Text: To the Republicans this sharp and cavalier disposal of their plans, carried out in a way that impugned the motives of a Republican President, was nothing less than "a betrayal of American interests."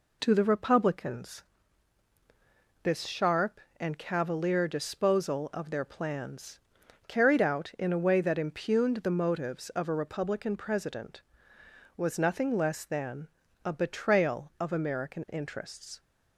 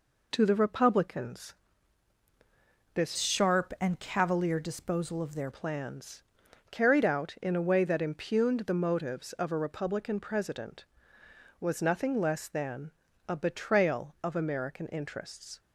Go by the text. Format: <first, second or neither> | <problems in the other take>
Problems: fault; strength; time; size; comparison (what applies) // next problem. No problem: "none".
first | pauses between "Republicans" and "this"; strong; at 1.5 s; 1.4 s long; strong in the first // changes voice from "sharp" to "their"; from 3.1 to 5.4 s; 2.3 s long // pauses between "than" and "a"; slight; at 12.9 s; 0.36 s long; slight in the first